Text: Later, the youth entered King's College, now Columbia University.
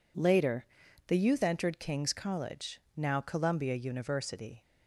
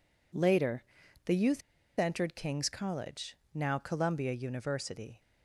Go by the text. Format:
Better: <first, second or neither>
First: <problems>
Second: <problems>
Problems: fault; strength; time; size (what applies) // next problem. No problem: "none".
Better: first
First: none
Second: pauses between "youth" and "entered"; at 1.6 s; 0.36 s long